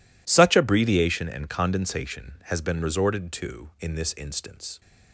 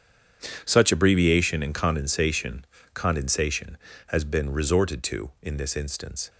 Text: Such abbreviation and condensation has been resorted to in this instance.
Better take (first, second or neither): first